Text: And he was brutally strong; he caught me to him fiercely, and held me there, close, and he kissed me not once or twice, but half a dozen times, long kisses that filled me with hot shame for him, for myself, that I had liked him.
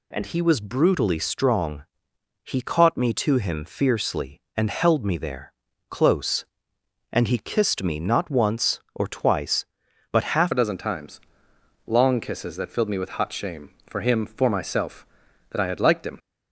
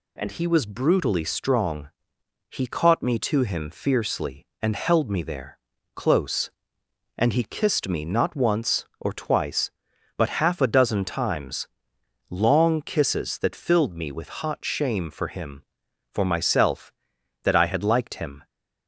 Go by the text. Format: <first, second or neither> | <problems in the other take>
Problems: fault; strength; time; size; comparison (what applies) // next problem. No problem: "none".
second | changes voice at "a"; from 10.5 s on; 5.6 s long